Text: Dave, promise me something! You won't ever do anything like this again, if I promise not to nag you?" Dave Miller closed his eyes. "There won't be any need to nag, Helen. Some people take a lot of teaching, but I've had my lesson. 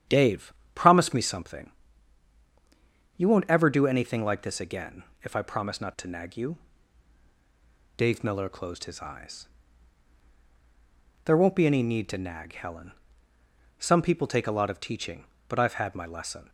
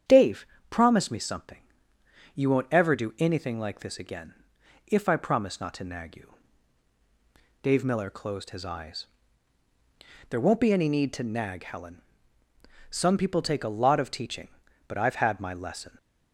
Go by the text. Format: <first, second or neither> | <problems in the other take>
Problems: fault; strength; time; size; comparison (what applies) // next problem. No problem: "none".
neither | starts louder than the rest; strong; the same in both